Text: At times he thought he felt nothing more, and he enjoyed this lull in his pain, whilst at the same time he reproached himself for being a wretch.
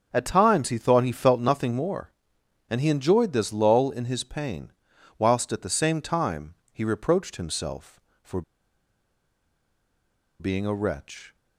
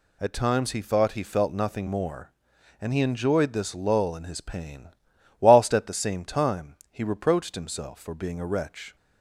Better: second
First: starts louder than the rest; until 1.1 s; 7 dB // pauses between "time" and "he"; slight; at 6.5 s; 0.18 s long // pauses between "for" and "being"; strong; at 8.4 s; 1.9 s long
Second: none

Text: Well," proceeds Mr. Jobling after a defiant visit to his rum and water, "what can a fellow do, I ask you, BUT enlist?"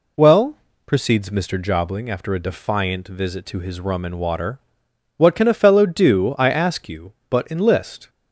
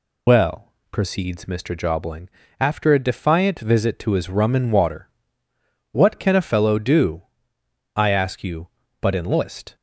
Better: first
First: none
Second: loses the start of "Well"; at 0.2 s; 80 ms // pauses between "Jobling" and "after"; slight; at 2.2 s; 0.30 s long

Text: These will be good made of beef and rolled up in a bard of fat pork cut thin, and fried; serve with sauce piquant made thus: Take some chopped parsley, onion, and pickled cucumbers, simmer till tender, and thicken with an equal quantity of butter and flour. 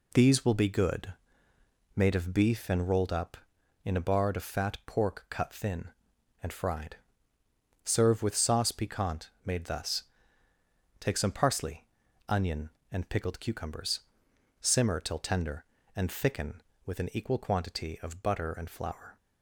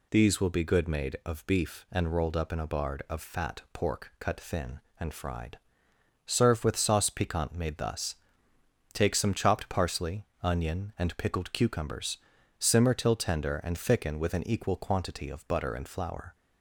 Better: second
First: pauses between "good" and "made"; noticeable; at 1.1 s; 0.82 s long // skips "chopped"; at 11.3 s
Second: none

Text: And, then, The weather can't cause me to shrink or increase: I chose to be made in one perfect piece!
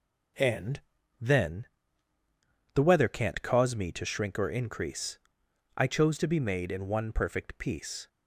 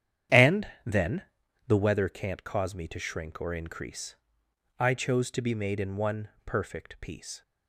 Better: first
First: none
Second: starts louder than the rest; strong; until 1.8 s; 9.5 dB // pauses between "one" and "perfect"; slight; at 6.2 s; 0.18 s long

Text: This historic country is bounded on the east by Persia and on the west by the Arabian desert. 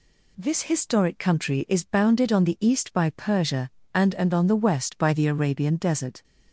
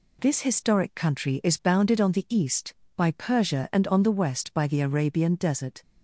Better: second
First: says "and" twice; at 4.1 s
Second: none

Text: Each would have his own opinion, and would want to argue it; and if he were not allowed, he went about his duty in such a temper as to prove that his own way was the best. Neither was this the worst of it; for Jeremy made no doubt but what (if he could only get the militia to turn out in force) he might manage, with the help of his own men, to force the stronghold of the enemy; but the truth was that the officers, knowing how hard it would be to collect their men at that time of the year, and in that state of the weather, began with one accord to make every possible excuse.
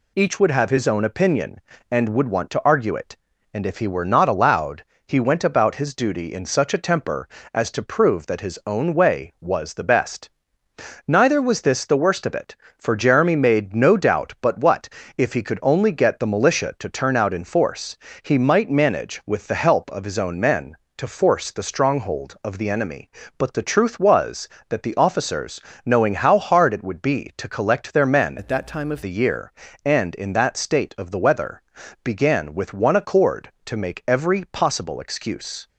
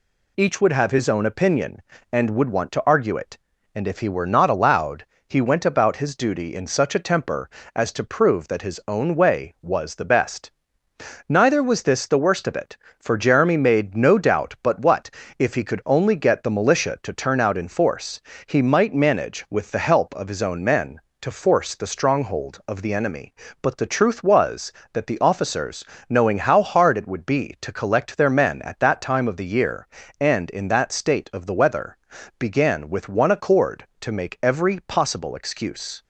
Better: second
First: changes voice from "at" to "of"; from 28.3 to 29.0 s; 0.7 s long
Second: none

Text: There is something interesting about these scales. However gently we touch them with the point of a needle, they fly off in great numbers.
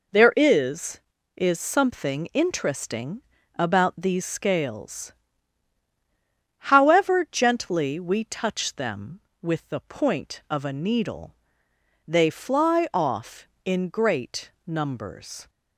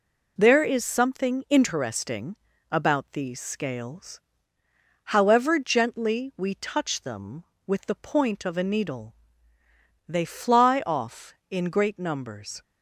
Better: second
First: says "is" twice; at 1.3 s // pauses between "interesting" and "about"; slight; at 3.2 s; 0.36 s long // pauses between "great" and "numbers"; slight; at 14.4 s; 0.16 s long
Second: pauses between "interesting" and "about"; slight; at 2.3 s; 0.36 s long

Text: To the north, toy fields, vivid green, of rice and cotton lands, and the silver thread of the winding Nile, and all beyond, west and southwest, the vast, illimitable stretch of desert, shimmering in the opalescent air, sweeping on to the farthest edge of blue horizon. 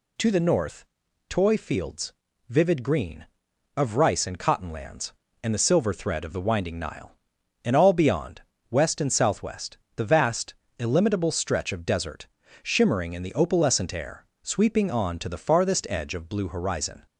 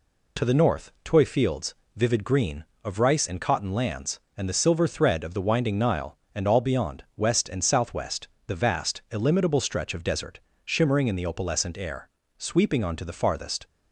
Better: first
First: none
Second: stops before "edge of blue horizon"; at 13.6 s

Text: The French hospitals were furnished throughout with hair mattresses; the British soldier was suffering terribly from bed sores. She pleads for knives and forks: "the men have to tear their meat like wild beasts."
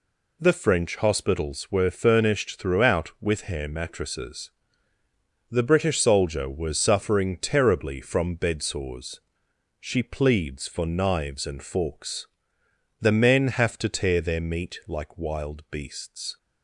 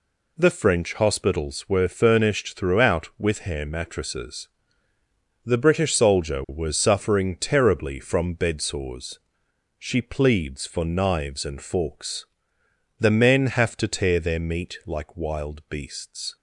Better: neither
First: none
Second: none

